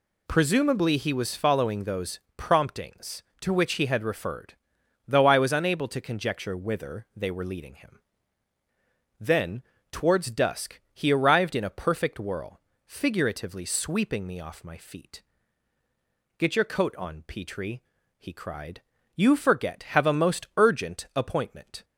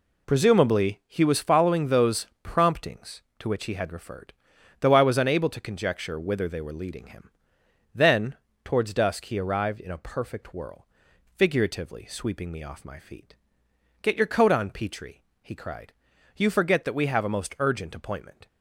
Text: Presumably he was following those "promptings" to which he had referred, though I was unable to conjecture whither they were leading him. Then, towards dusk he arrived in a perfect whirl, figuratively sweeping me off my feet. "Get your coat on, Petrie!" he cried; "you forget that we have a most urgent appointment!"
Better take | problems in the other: second | pauses between "those" and "promptings"; slight; at 2.1 s; 0.16 s long; slight in the second // skips "that we"; at 19.8 s

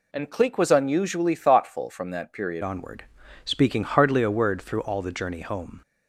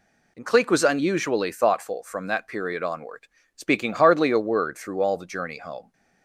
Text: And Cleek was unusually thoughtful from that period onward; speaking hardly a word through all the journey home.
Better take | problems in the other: second | changes voice at "onward"; from 2.6 s on; 3.2 s long

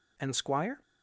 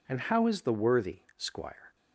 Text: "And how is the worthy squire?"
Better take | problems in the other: second | skips "how is the worthy"; at 0.3 s

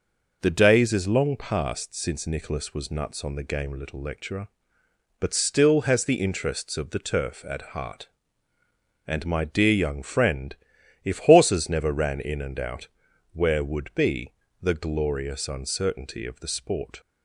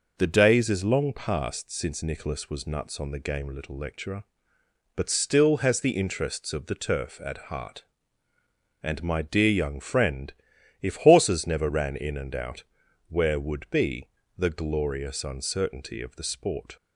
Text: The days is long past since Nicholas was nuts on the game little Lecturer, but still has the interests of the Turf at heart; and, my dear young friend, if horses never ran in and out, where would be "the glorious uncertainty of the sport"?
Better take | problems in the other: neither | pauses between "be" and "the"; slight; the same in both

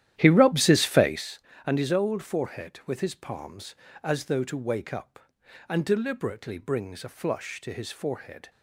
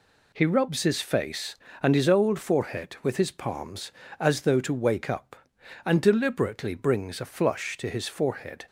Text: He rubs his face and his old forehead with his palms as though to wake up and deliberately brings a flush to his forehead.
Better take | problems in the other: second | starts louder than the rest; strong; until 1.3 s; 12 dB

